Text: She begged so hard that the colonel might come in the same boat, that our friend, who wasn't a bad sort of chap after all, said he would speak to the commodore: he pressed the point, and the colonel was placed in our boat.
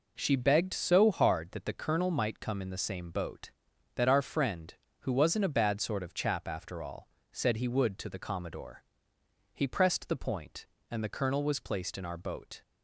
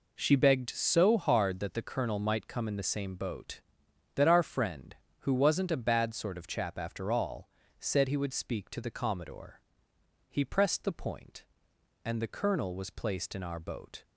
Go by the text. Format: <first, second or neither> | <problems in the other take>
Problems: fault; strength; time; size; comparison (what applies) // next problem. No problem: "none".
second | skips "speak"; at 7.9 s